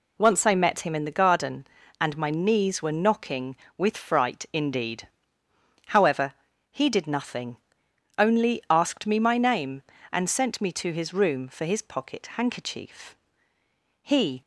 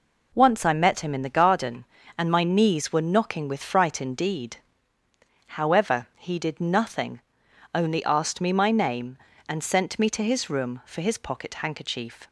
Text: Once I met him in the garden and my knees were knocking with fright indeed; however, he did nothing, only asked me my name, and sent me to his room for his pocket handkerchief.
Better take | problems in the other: second | goes on to say "He"; slight; from 14.0 s on; 0.40 s long

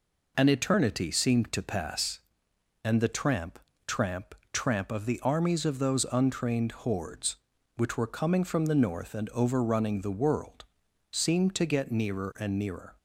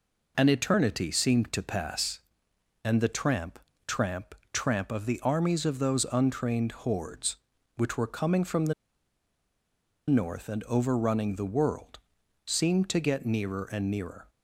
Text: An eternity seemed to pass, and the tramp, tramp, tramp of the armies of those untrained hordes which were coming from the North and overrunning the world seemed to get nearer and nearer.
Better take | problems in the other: first | pauses between "the" and "North"; strong; at 8.7 s; 1.3 s long // pauses between "world" and "seemed"; noticeable; at 11.9 s; 0.46 s long; noticeable in the first

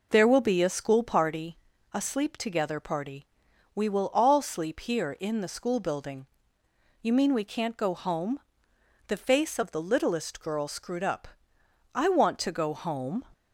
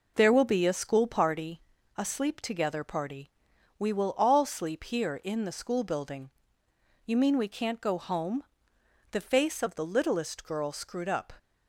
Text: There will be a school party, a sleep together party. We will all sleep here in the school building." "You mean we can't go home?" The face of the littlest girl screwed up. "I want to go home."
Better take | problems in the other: first | stops before "I want to go home"; at 11.3 s

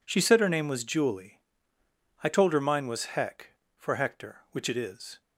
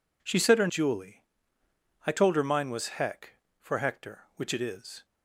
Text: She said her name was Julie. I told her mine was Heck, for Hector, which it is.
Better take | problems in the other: first | skips "name was"; at 0.6 s

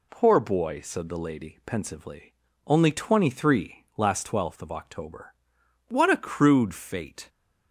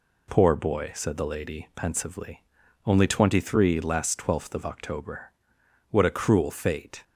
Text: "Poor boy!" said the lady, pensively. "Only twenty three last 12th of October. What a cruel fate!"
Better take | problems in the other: second | says "crude" for "cruel"; at 6.1 s

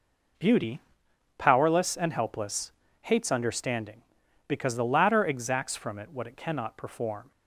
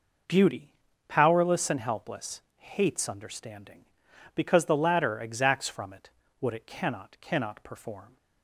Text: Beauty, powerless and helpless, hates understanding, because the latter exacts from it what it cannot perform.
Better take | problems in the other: first | pauses between "it" and "what"; slight; at 6.0 s; 0.32 s long // says "cannot" twice; at 7.2 s

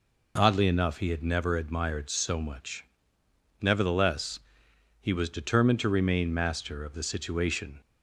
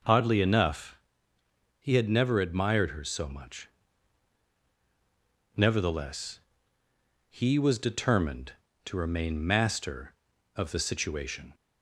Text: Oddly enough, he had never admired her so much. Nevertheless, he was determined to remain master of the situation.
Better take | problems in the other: second | skips "her"; at 2.1 s

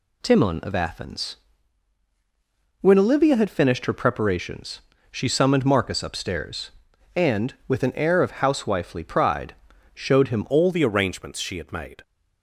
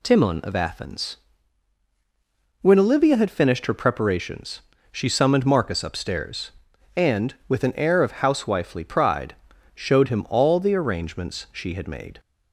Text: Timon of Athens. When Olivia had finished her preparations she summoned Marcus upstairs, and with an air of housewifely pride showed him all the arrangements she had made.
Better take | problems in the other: second | pauses between "preparations" and "she"; slight; at 4.8 s; 0.32 s long; slight in the second // pauses between "pride" and "showed"; at 9.5 s; 0.38 s long; also in the second // changes voice at "all"; from 10.4 s on; 1.6 s long

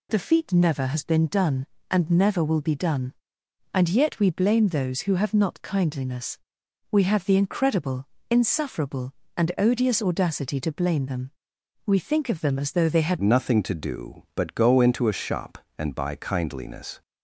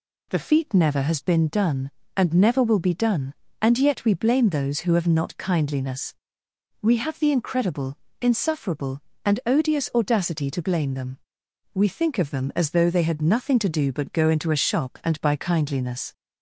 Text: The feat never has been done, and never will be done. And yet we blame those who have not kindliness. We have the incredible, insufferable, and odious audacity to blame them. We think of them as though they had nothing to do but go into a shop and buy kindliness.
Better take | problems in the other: second | changes voice at "nothing"; from 13.2 s on; 3.8 s long

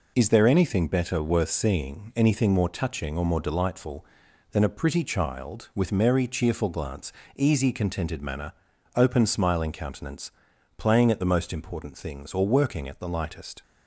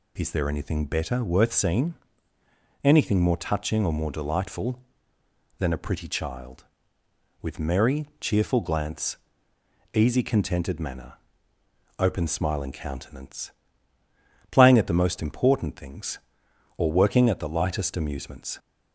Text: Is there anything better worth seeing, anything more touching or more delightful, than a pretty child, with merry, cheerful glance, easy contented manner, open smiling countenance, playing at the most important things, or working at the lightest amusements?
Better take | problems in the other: second | stops before "amusements"; at 13.6 s

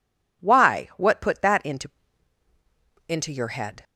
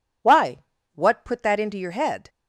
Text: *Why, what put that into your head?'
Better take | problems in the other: second | says "into" twice; at 3.0 s

